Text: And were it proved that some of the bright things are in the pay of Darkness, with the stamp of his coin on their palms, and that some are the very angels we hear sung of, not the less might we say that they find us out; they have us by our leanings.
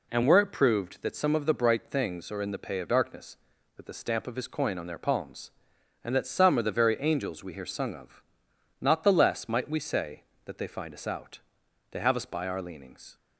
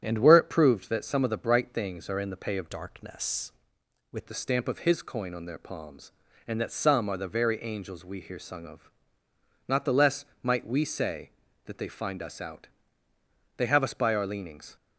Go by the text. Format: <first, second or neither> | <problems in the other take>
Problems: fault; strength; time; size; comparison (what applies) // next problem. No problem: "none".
first | starts louder than the rest; strong; until 1.0 s; 9 dB // changes voice from "Darkness" to "with"; from 2.6 to 4.2 s; 1.6 s long // pauses between "less" and "might"; slight; at 10.2 s; 0.16 s long